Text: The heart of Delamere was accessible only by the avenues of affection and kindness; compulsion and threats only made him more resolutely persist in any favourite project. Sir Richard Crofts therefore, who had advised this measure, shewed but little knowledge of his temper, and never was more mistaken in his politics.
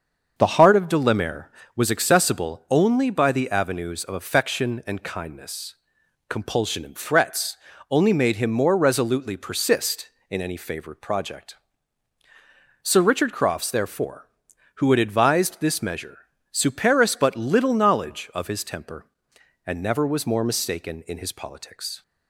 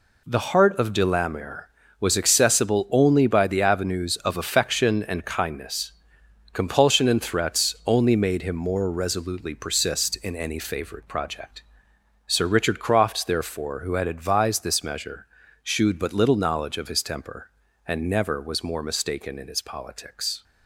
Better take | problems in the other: second | starts louder than the rest; until 1.3 s; 7 dB // pauses between "threats" and "only"; slight; at 7.5 s; 0.34 s long // says "superis" for "shewed"; at 16.5 s

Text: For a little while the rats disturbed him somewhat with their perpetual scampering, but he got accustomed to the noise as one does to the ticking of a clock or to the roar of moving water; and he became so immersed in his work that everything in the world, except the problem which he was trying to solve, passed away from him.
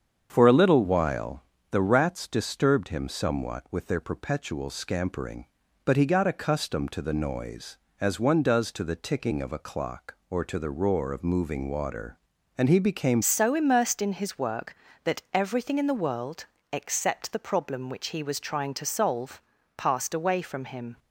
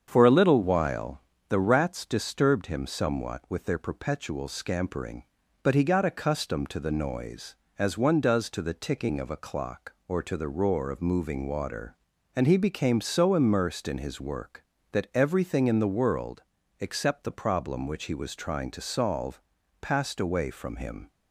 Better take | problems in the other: second | starts louder than the rest; strong; until 1.3 s; 7.5 dB; strong in the second // pauses between "while" and "the"; slight; at 1.4 s; 0.28 s long; slight in the second // changes voice at "so"; from 13.2 s on; 7.7 s long

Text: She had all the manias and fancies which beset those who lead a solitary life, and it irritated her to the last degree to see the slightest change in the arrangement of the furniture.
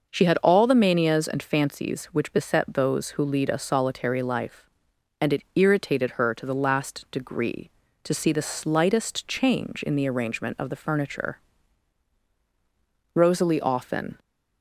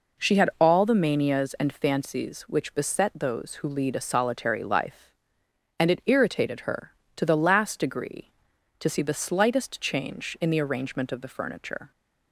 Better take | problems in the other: second | starts louder than the rest; noticeable; until 1.1 s; 6 dB // goes on to say "Rosalie often"; noticeable; from 13.1 s on; 1.0 s long

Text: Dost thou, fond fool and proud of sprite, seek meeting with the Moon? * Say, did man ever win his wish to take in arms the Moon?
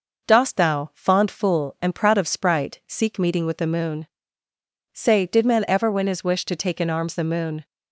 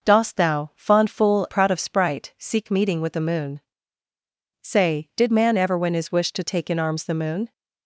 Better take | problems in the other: first | skips "and"; at 1.4 s

